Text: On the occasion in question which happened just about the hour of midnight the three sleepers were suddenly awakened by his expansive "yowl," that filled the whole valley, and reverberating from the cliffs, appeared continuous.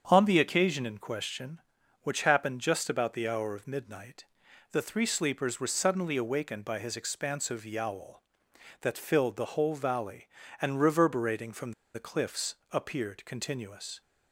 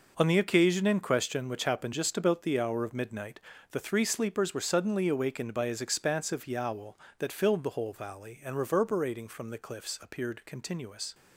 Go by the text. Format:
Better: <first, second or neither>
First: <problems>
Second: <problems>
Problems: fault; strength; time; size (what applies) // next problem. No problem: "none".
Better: second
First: starts louder than the rest; strong; until 1.0 s; 7.5 dB // pauses between "midnight" and "the"; noticeable; at 4.2 s; 0.46 s long // pauses between "from" and "the"; slight; at 11.7 s; 0.22 s long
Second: pauses between "midnight" and "the"; slight; at 3.3 s; 0.32 s long